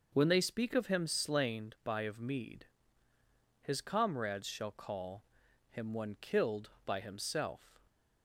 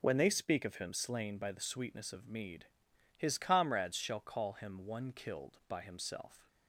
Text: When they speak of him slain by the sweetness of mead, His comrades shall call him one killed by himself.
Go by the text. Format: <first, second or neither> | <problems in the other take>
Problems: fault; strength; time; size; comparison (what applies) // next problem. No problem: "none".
second | skips "the sweetness"; at 2.0 s // pauses between "call" and "him"; noticeable; at 5.2 s; 0.48 s long